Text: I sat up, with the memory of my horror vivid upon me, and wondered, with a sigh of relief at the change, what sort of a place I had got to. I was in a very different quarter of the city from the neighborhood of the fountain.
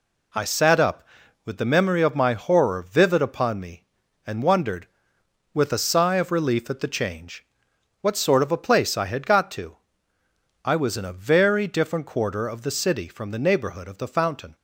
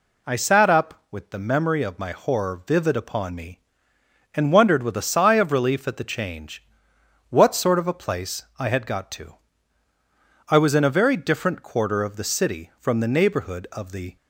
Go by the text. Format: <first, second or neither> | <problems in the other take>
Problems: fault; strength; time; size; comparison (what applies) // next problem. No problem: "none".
first | pauses between "place" and "I"; slight; at 8.4 s; 0.16 s long // stops before "fountain"; at 14.1 s